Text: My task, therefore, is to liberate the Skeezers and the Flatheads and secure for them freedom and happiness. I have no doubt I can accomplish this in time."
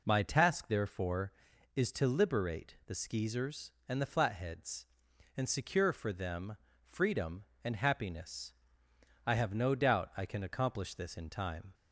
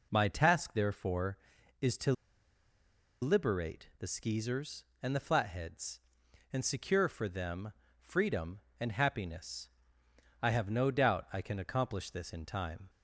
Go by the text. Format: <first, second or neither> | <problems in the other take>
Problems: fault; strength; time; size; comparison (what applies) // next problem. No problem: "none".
first | pauses between "to" and "liberate"; at 2.1 s; 1.0 s long // pauses between "them" and "freedom"; slight; at 7.7 s; 0.30 s long; slight in the first